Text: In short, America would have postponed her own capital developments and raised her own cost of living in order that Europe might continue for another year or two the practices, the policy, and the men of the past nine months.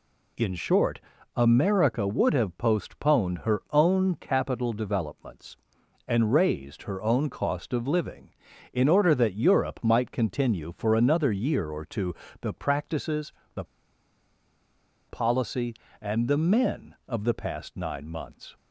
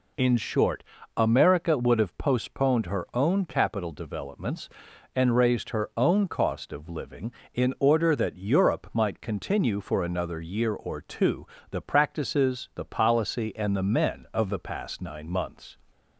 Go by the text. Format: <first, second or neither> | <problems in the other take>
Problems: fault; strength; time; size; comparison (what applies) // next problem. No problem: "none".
second | pauses between "two" and "the"; slight; at 12.1 s; 0.28 s long; slight in the second // pauses between "the" and "policy"; strong; at 13.6 s; 1.4 s long